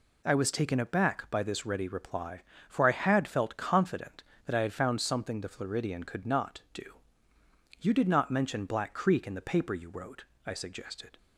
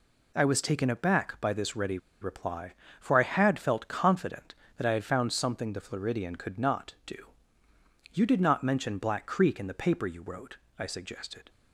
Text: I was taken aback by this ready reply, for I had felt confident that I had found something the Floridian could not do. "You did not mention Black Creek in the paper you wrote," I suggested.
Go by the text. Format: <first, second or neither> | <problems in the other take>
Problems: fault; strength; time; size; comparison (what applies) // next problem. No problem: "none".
first | pauses between "ready" and "reply"; slight; at 1.9 s; 0.22 s long